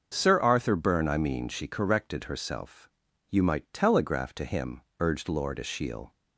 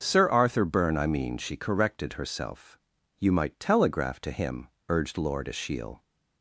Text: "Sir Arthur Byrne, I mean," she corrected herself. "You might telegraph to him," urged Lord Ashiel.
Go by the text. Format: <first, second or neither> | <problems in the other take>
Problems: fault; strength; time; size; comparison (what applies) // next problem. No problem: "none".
neither | starts louder than the rest; the same in both